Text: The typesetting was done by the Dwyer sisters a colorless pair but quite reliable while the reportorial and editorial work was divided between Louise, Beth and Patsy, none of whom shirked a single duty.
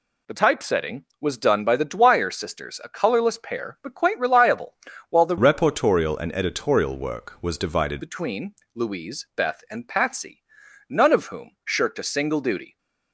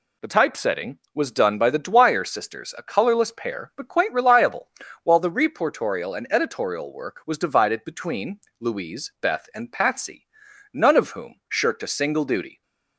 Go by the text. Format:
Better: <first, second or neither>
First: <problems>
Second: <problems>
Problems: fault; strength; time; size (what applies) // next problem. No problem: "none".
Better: second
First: pauses between "reliable" and "while"; slight; at 4.7 s; 0.36 s long // changes voice from "reportorial" to "divided"; from 5.3 to 8.0 s; 2.7 s long // pauses between "between" and "Louise"; slight; at 8.5 s; 0.20 s long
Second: pauses between "reliable" and "while"; slight; at 4.6 s; 0.36 s long // pauses between "between" and "Louise"; slight; at 8.3 s; 0.20 s long